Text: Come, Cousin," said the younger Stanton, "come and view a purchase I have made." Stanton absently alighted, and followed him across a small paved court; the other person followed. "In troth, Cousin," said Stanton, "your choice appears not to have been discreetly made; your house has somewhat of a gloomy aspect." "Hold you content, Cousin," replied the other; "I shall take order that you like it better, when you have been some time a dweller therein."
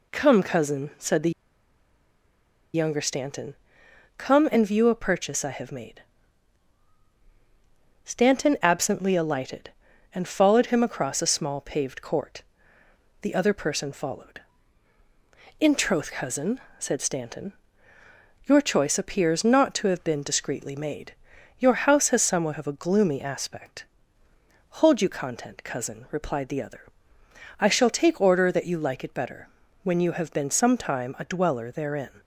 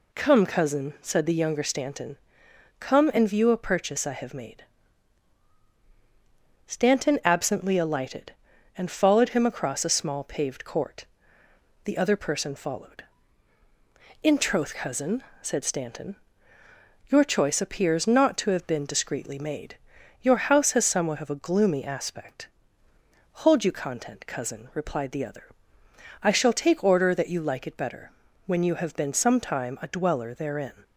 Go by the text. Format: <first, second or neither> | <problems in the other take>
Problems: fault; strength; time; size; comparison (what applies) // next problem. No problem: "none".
second | pauses between "the" and "younger"; strong; at 1.3 s; 1.4 s long